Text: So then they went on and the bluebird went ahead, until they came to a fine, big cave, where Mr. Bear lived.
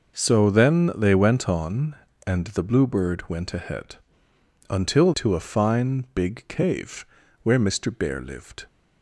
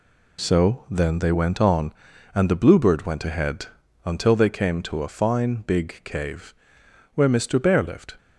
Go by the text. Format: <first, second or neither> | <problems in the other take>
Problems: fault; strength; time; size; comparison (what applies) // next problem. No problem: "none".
second | skips "they came"; at 5.1 s